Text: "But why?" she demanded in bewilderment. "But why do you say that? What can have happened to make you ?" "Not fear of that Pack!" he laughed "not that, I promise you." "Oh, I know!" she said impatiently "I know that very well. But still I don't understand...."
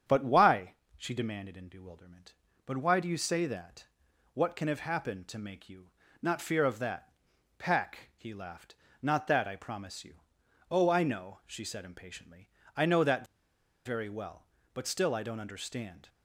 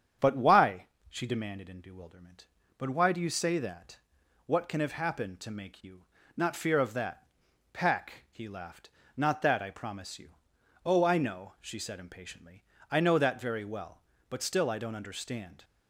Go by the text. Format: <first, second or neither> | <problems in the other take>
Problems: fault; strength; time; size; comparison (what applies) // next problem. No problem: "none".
second | starts louder than the rest; strong; until 1.2 s; 8.5 dB; strong in the second // pauses between "that" and "Pack"; noticeable; at 7.1 s; 0.46 s long; noticeable in the second // pauses between "laughed" and "not"; slight; at 8.7 s; 0.28 s long; slight in the second // pauses between "impatiently" and "I"; slight; at 12.4 s; 0.26 s long; slight in the second // pauses between "that" and "very"; noticeable; at 13.2 s; 0.59 s long